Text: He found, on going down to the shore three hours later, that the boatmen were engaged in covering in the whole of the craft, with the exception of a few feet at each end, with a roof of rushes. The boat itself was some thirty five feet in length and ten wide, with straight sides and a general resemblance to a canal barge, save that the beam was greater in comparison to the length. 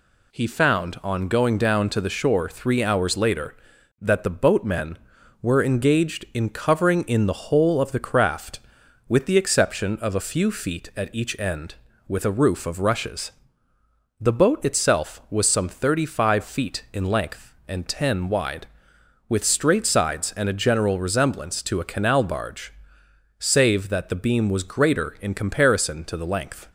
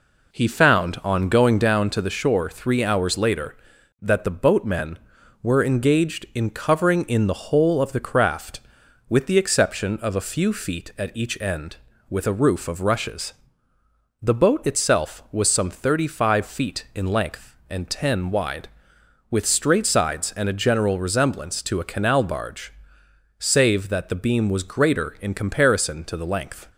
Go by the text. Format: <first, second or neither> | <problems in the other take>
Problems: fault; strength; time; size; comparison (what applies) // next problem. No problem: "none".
first | starts louder than the rest; until 1.8 s; 4 dB